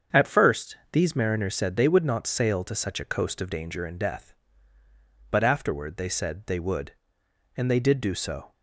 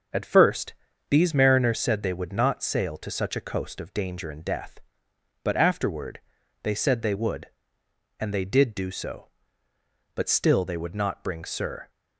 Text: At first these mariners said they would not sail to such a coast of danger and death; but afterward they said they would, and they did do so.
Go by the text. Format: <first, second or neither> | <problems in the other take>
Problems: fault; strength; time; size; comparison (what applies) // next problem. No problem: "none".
first | starts louder than the rest; until 1.4 s; 6.5 dB; strong in the first // pauses between "first" and "these"; slight; at 0.7 s; 0.36 s long; slight in the first // pauses between "afterward" and "they"; at 6.1 s; 0.44 s long // goes on to say "But still they would not bring Sir"; strong; from 10.1 s on; 1.7 s long